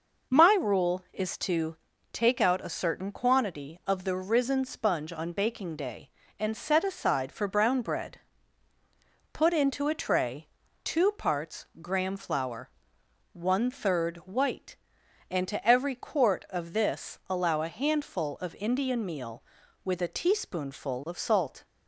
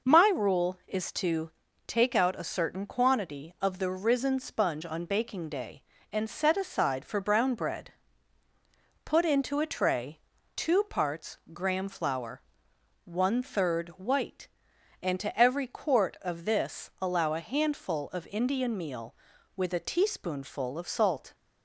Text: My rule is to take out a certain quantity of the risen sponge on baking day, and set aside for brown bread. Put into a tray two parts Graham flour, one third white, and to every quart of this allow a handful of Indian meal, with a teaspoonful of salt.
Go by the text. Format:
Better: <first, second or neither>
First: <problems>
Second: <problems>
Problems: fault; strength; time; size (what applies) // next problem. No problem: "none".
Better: neither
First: pauses between "to" and "take"; slight; at 1.7 s; 0.36 s long // pauses between "tray" and "two"; at 10.4 s; 0.38 s long // pauses between "parts" and "Graham"; slight; at 11.6 s; 0.16 s long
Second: pauses between "to" and "take"; slight; at 1.5 s; 0.36 s long // pauses between "tray" and "two"; at 10.1 s; 0.38 s long // pauses between "parts" and "Graham"; slight; at 11.3 s; 0.16 s long